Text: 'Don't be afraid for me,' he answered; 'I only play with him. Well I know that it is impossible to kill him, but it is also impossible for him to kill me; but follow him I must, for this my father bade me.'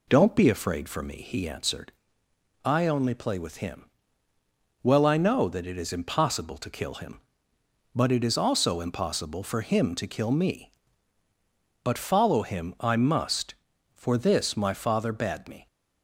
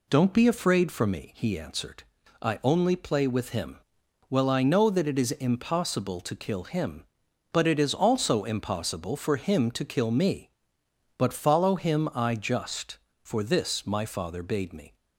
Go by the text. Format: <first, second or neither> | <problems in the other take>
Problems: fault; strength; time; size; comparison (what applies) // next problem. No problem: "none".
first | says "just" for "must"; at 12.3 s